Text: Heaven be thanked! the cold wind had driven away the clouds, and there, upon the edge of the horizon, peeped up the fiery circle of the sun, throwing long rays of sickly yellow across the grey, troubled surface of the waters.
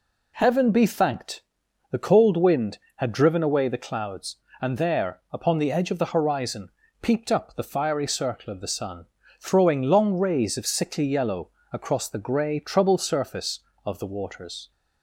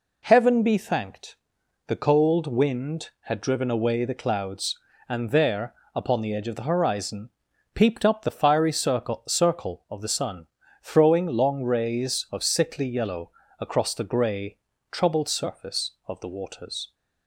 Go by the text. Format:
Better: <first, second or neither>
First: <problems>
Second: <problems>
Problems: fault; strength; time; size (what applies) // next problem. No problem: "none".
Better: first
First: pauses between "yellow" and "across"; slight; at 11.5 s; 0.20 s long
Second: says "circle" twice; at 9.2 s // pauses between "yellow" and "across"; slight; at 13.3 s; 0.28 s long